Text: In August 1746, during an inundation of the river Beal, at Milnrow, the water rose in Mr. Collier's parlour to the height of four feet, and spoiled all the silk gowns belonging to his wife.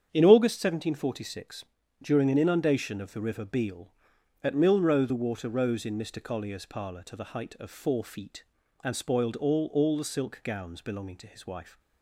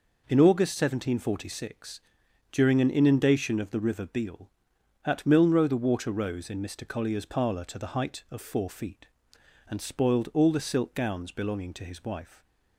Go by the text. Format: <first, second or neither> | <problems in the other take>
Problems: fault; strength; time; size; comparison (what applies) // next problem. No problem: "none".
second | starts louder than the rest; strong; until 1.1 s; 8 dB // says "all" twice; at 9.7 s